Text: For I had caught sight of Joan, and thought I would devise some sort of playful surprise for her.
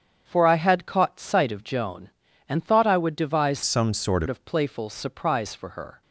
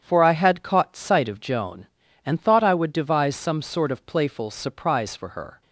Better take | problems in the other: second | starts louder than the rest; strong; until 1.2 s; 8 dB; strong in the second // changes voice from "some" to "sort"; from 3.6 to 4.2 s; 0.6 s long

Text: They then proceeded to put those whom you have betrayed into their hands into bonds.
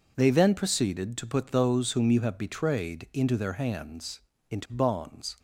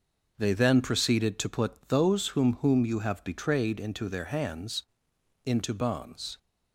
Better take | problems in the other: first | says "whom" twice; at 2.6 s // pauses between "hands" and "into"; noticeable; at 4.8 s; 0.62 s long; slight in the first

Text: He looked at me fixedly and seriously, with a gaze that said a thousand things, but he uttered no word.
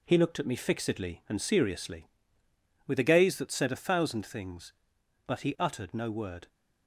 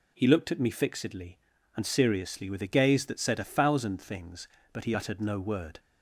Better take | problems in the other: second | gets quieter; noticeable; throughout; 5 dB

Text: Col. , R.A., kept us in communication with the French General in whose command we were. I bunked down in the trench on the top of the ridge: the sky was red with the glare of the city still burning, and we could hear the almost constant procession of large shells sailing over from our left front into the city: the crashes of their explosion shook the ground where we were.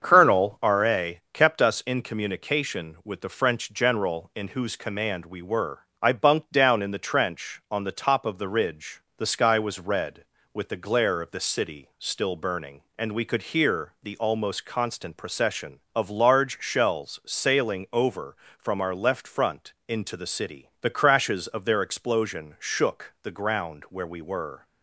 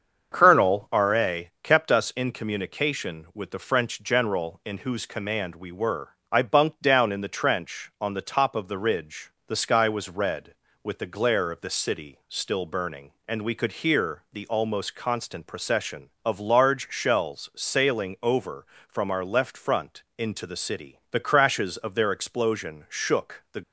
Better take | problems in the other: first | starts louder than the rest; until 1.3 s; 7 dB; also in the first // pauses between "front" and "into"; slight; at 20.0 s; 0.16 s long; slight in the first // stops before "ground where we were"; at 23.6 s

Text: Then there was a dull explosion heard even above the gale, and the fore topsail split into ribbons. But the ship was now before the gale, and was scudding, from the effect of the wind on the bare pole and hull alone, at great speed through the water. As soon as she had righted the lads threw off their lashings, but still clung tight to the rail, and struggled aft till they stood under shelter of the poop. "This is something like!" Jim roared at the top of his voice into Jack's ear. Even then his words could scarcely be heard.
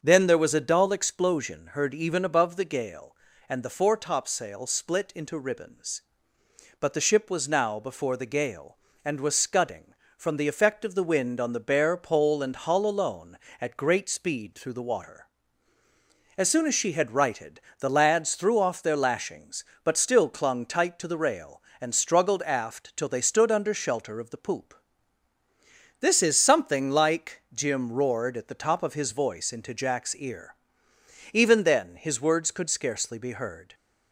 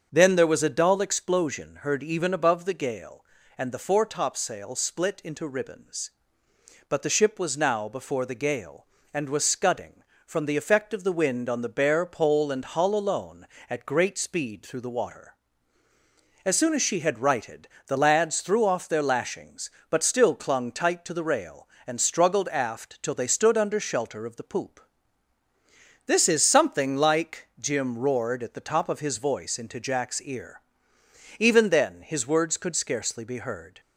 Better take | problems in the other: neither | starts louder than the rest; the same in both // pauses between "righted" and "the"; slight; the same in both

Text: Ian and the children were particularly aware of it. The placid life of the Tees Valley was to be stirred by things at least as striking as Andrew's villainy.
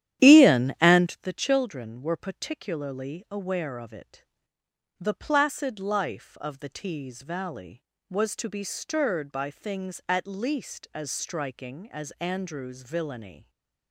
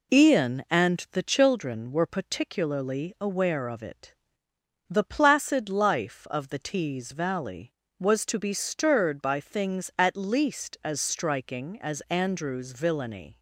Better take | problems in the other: second | starts louder than the rest; strong; until 1.2 s; 11 dB // stays silent after the last word; slight; from 13.3 s on; 0.6 s long

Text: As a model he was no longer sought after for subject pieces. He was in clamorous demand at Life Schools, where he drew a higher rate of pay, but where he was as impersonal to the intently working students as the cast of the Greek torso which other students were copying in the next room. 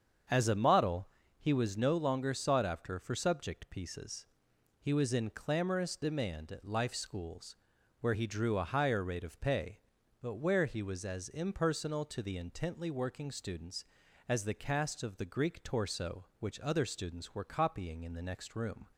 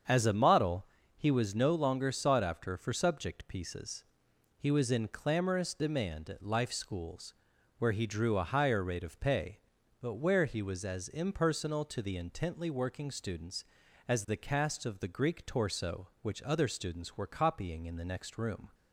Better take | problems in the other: neither | starts louder than the rest; strong; the same in both // pauses between "model" and "he"; slight; the same in both

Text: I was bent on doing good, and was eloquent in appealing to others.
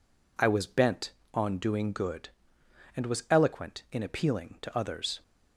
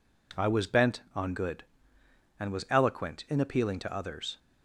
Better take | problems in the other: first | skips "doing"; at 1.3 s

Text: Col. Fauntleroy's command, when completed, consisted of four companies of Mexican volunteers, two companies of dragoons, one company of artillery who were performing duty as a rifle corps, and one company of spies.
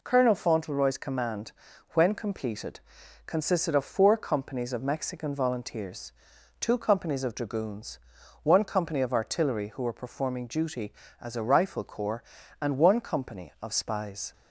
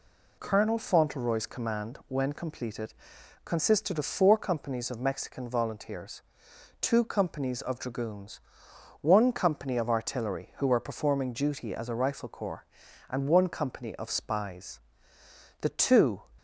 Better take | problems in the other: first | goes on to say "The two"; from 15.6 s on; 0.60 s long

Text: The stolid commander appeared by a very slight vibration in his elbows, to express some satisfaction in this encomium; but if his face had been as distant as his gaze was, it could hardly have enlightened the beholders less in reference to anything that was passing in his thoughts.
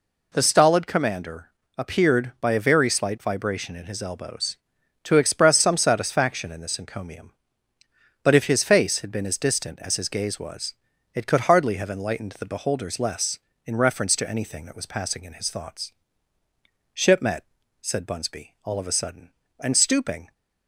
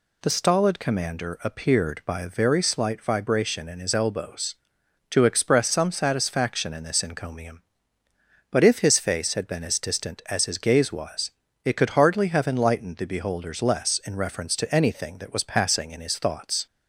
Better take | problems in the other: second | pauses between "commander" and "appeared"; slight; at 1.5 s; 0.26 s long // goes on to say "Shipmet said Bunsby all of a sudden and stooping"; strong; from 16.9 s on; 3.3 s long

